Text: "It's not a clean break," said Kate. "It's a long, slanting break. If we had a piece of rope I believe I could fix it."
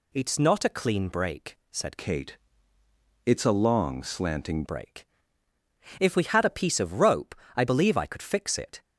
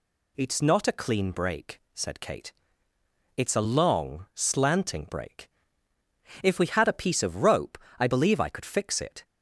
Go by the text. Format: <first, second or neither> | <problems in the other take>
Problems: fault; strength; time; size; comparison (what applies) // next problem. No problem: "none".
second | changes voice from "Kate" to "slanting"; from 1.9 to 4.6 s; 2.7 s long // pauses between "rope" and "I"; slight; at 7.3 s; 0.22 s long; slight in the second